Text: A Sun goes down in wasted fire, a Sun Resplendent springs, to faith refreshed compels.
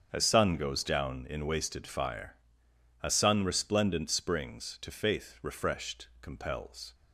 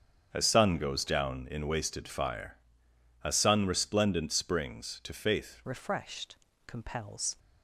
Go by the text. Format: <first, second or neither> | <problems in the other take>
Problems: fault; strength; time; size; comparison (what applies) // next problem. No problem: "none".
first | starts louder than the rest; strong; until 1.3 s; 7.5 dB; strong in the first // changes voice at "refreshed"; from 5.6 s on; 1.7 s long // pauses between "refreshed" and "compels"; slight; at 6.3 s; 0.30 s long; slight in the first